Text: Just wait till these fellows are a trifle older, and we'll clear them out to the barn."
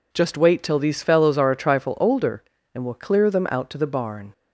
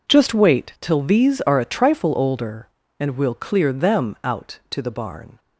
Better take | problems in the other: first | skips "fellows"; at 1.4 s

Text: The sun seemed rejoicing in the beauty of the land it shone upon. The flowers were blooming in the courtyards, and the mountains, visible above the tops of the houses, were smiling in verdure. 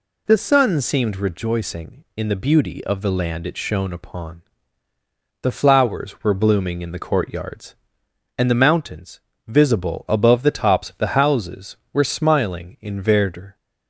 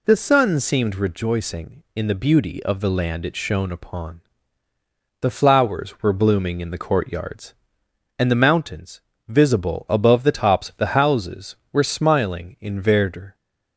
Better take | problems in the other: neither | none

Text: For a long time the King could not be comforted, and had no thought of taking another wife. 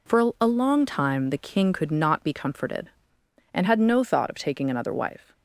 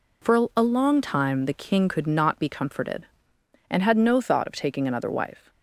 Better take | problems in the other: neither | none

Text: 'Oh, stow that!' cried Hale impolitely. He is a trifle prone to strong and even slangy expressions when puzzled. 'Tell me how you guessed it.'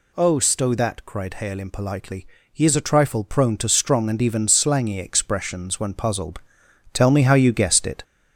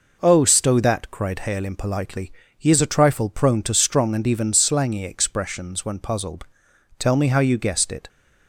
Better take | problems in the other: second | gets louder; throughout; 4 dB

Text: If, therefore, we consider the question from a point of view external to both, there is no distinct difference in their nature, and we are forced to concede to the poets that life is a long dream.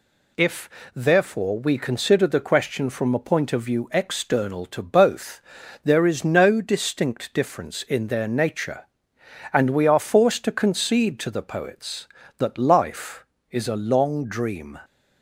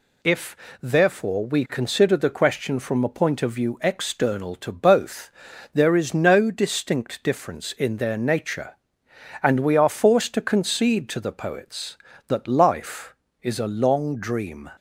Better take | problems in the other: neither | none

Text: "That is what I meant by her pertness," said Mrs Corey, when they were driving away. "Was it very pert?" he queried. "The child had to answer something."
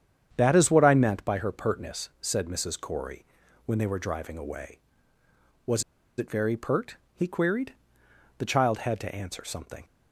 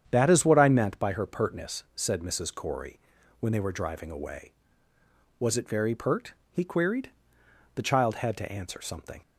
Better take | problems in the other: second | starts louder than the rest; strong; until 1.3 s; 8.5 dB; strong in the second // pauses between "Was" and "it"; slight; at 5.8 s; 0.35 s long

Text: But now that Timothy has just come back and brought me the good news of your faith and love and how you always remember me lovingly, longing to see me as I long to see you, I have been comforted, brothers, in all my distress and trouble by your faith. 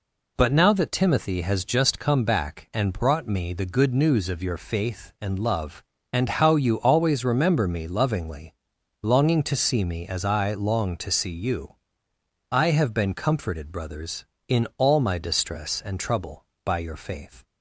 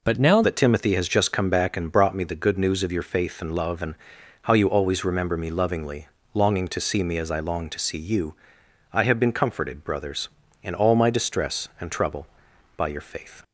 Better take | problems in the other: first | changes voice at "that"; from 0.4 s on; 13.0 s long // pauses between "and" and "how"; noticeable; at 3.9 s; 0.48 s long

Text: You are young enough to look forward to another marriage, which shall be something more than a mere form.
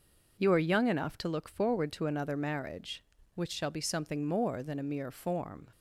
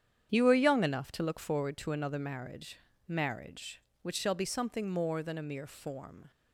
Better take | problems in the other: first | starts louder than the rest; strong; until 1.3 s; 9 dB // says "marriage" twice; at 3.0 s

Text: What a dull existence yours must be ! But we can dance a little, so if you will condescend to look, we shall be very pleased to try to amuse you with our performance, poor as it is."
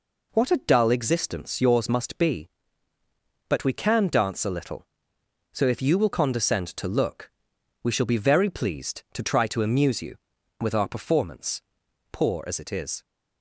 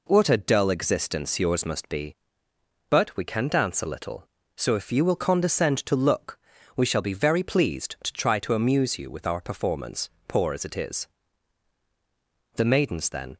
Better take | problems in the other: first | goes on to say "The maidens then"; noticeable; from 12.5 s on; 0.82 s long

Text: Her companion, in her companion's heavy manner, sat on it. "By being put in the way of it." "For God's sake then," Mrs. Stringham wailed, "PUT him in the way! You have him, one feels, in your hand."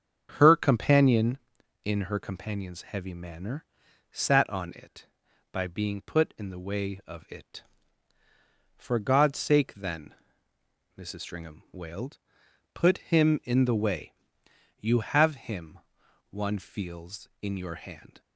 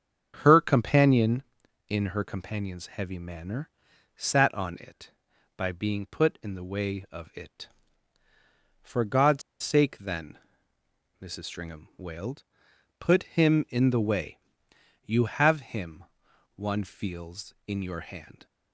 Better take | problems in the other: first | starts louder than the rest; strong; until 1.4 s; 7.5 dB; strong in the first // pauses between "God's" and "sake"; slight; at 9.4 s; 0.21 s long

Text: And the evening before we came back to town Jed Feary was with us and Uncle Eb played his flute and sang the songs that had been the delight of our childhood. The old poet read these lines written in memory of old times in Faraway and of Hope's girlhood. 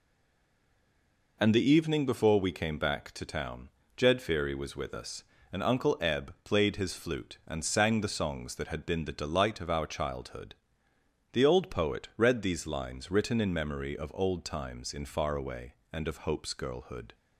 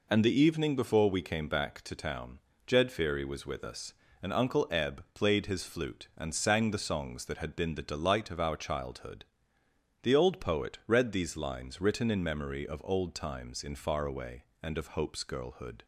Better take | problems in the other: second | stays silent before the first word; noticeable; until 1.3 s; 1.3 s long // pauses between "town" and "Jed"; slight; at 3.6 s; 0.28 s long; slight in the second

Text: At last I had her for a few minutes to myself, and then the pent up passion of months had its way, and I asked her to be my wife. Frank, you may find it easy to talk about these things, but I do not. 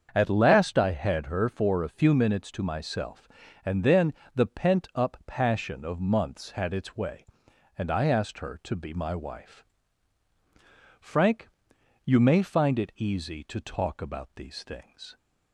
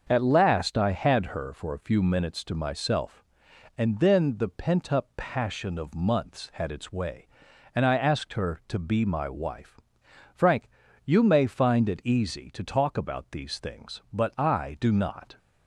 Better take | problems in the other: second | starts louder than the rest; until 1.1 s; 7 dB; also in the second // pauses between "then" and "the"; slight; at 4.1 s; 0.22 s long // stops before "but I do not"; at 15.1 s

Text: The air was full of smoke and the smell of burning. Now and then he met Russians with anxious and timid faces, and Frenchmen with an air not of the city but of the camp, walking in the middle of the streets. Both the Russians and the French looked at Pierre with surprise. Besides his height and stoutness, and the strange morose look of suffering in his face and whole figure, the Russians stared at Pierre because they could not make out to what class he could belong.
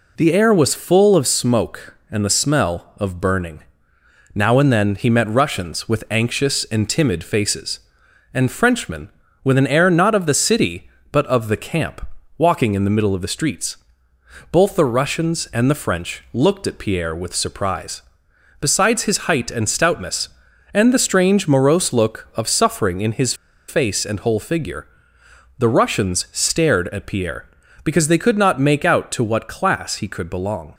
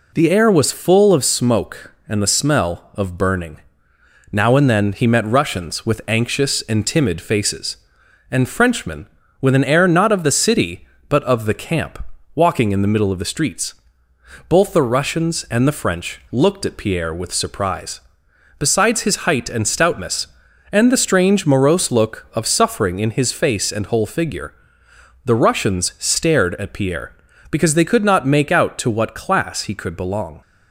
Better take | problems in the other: second | pauses between "his" and "face"; slight; at 23.3 s; 0.33 s long

